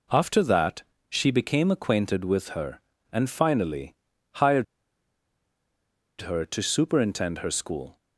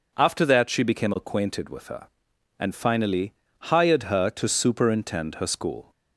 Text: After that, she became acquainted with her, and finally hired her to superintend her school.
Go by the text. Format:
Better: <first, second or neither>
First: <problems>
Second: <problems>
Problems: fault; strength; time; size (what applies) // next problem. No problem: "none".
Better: second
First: pauses between "finally" and "hired"; at 3.9 s; 0.42 s long // pauses between "hired" and "her"; strong; at 4.6 s; 1.5 s long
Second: pauses between "finally" and "hired"; at 3.3 s; 0.38 s long